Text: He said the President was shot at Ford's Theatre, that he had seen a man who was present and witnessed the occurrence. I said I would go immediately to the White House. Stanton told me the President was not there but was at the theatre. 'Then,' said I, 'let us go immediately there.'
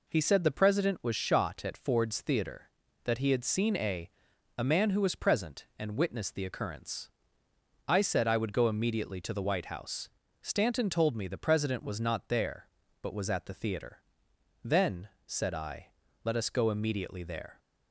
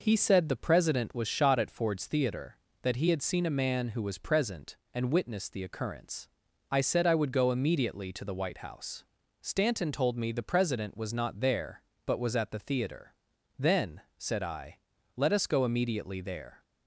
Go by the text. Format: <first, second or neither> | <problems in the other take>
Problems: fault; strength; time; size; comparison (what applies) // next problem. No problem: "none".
second | says "a" twice; at 4.5 s